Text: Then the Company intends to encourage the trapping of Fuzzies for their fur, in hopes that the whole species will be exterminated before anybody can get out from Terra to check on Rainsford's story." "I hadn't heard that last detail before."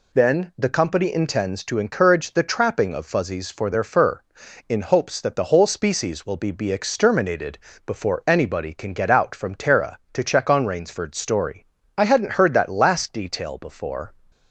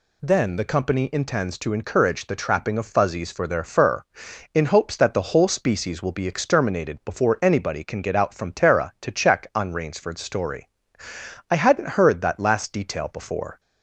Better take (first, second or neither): second